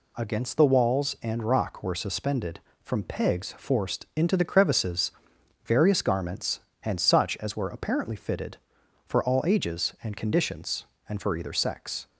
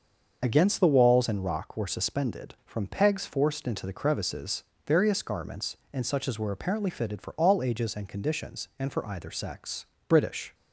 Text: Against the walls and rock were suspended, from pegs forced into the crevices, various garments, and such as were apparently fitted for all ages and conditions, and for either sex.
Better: first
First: none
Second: starts louder than the rest; until 1.4 s; 6.5 dB // goes on to say "British"; slight; from 10.0 s on; 0.46 s long

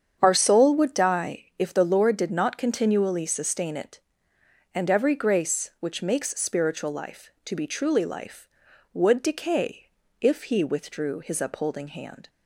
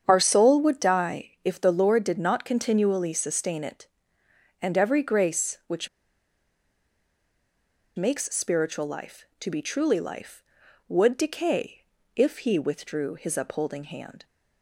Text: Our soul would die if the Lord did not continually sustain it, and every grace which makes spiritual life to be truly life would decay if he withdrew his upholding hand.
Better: first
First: starts louder than the rest; strong; until 1.2 s; 8 dB // pauses between "die" and "if"; slight; at 1.4 s; 0.16 s long // pauses between "decay" and "if"; slight; at 9.8 s; 0.34 s long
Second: starts louder than the rest; strong; until 1.0 s; 8 dB // pauses between "die" and "if"; slight; at 1.2 s; 0.16 s long // pauses between "which" and "makes"; strong; at 5.8 s; 2.0 s long // pauses between "decay" and "if"; slight; at 11.8 s; 0.34 s long

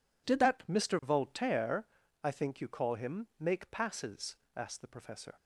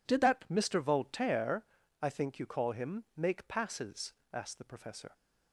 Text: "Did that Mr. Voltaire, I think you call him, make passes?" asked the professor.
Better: neither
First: none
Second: none

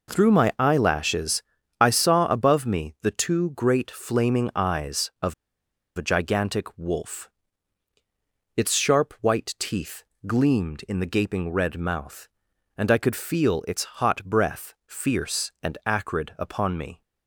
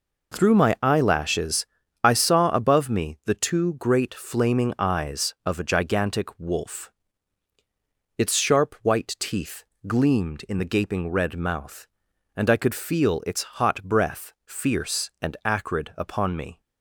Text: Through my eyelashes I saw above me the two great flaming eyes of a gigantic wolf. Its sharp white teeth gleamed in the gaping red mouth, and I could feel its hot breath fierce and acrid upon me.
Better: second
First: pauses between "eyelashes" and "I"; slight; at 1.4 s; 0.36 s long // pauses between "of" and "a"; noticeable; at 5.3 s; 0.63 s long // pauses between "teeth" and "gleamed"; slight; at 10.0 s; 0.20 s long // pauses between "its" and "hot"; slight; at 13.8 s; 0.16 s long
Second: pauses between "eyelashes" and "I"; slight; at 1.6 s; 0.36 s long // pauses between "teeth" and "gleamed"; slight; at 9.6 s; 0.20 s long // pauses between "its" and "hot"; slight; at 13.4 s; 0.16 s long

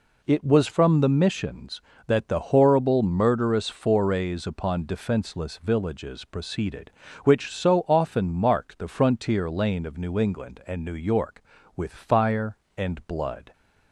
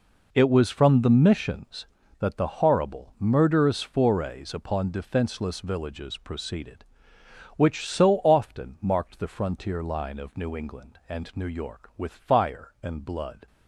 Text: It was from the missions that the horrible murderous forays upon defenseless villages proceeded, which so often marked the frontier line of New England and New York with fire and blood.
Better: second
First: says "lane" for "line"; at 9.5 s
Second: none

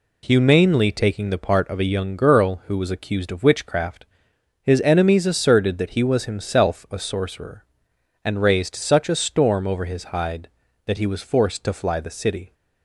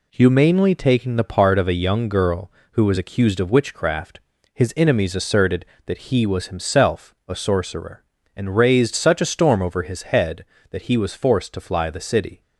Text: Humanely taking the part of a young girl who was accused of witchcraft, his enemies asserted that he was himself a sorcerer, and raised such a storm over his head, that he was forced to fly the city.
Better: second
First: says "hide" for "head"; at 10.1 s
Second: none

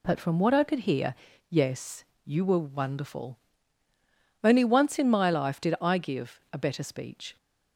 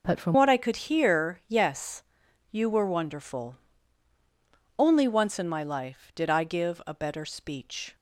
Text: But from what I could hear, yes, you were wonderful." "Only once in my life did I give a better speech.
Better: first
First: none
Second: changes voice at "what"; from 0.3 s on; 7.6 s long

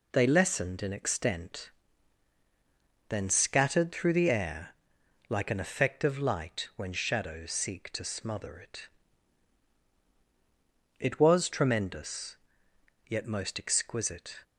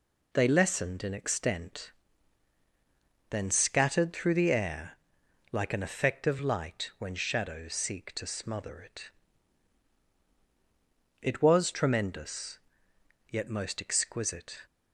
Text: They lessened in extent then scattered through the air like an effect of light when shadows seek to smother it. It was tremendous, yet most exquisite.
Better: neither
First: pauses between "extent" and "then"; strong; at 1.6 s; 1.4 s long // pauses between "air" and "like"; noticeable; at 4.7 s; 0.56 s long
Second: pauses between "extent" and "then"; strong; at 1.8 s; 1.4 s long // pauses between "air" and "like"; noticeable; at 4.9 s; 0.56 s long

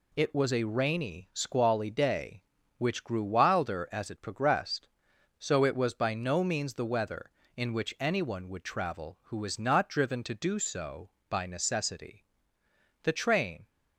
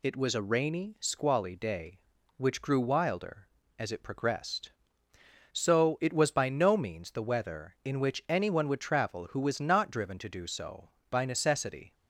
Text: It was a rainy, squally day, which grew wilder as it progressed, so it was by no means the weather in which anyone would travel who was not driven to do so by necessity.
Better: second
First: goes on to say "The train"; noticeable; from 13.0 s on; 0.64 s long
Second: none

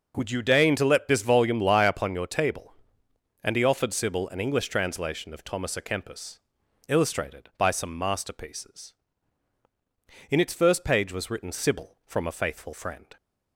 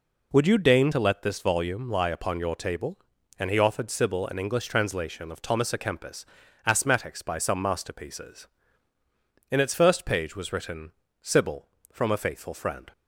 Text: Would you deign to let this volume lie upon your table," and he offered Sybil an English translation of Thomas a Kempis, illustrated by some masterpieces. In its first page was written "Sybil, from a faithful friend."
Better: first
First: none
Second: says "asthmatics" for "illustrated"; at 6.6 s // pauses between "written" and "Sybil"; slight; at 10.9 s; 0.28 s long

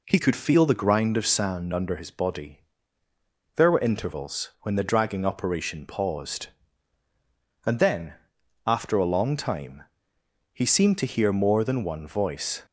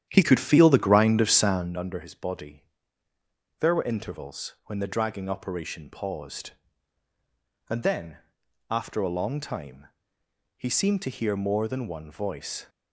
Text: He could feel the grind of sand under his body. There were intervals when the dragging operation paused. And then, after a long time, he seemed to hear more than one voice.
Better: first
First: none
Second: starts louder than the rest; strong; until 1.8 s; 10 dB

